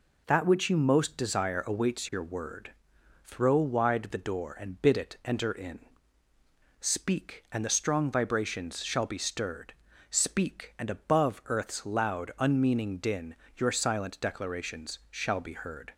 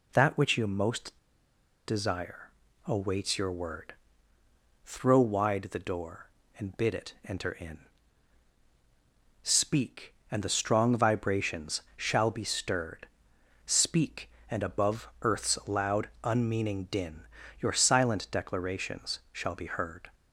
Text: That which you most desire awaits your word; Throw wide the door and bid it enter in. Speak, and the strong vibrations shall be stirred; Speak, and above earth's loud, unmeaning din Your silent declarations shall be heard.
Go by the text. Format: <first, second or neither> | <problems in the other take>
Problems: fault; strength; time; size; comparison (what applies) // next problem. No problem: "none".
first | pauses between "most" and "desire"; noticeable; at 1.1 s; 0.70 s long // pauses between "desire" and "awaits"; slight; at 2.5 s; 0.34 s long // pauses between "vibrations" and "shall"; slight; at 11.8 s; 0.16 s long // pauses between "din" and "Your"; slight; at 17.2 s; 0.36 s long; slight in the first